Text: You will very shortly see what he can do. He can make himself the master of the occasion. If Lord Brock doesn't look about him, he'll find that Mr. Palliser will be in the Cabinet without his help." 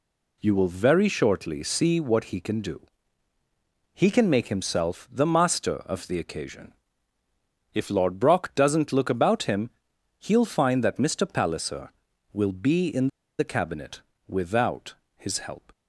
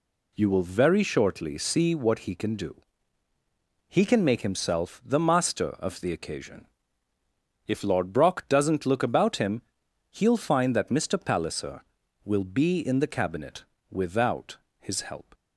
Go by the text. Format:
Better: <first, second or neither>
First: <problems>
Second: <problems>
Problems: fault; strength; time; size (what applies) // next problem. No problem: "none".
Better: second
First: pauses between "in" and "the"; slight; at 13.0 s; 0.30 s long // pauses between "Cabinet" and "without"; slight; at 14.0 s; 0.26 s long // pauses between "without" and "his"; slight; at 14.9 s; 0.22 s long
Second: pauses between "Cabinet" and "without"; slight; at 13.6 s; 0.26 s long // pauses between "without" and "his"; slight; at 14.5 s; 0.22 s long